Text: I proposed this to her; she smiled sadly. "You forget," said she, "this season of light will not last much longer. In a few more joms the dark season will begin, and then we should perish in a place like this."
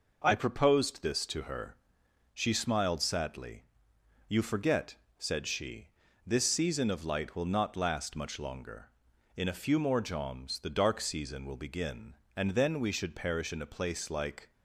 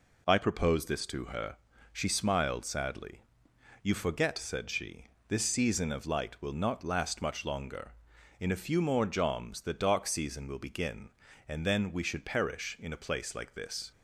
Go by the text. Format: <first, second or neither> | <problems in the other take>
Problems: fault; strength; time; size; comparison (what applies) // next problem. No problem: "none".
second | stops before "this"; at 14.5 s